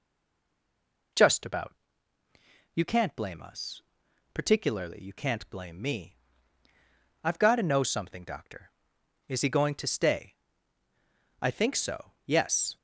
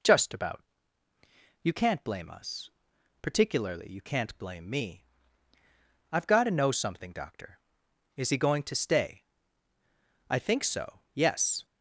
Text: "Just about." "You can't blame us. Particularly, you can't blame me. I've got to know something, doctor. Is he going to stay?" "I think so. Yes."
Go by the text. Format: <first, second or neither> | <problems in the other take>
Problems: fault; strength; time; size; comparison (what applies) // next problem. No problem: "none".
second | stays silent before the first word; until 1.1 s; 1.1 s long